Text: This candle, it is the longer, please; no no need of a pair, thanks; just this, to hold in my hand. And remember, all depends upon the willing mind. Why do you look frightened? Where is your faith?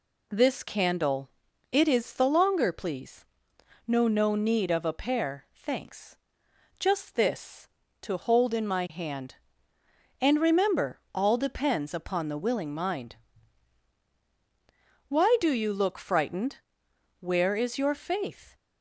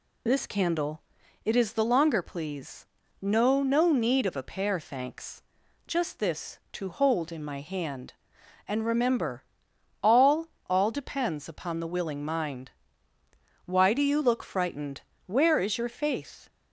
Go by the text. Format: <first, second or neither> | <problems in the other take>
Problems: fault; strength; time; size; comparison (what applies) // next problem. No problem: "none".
first | says "all" twice; at 10.6 s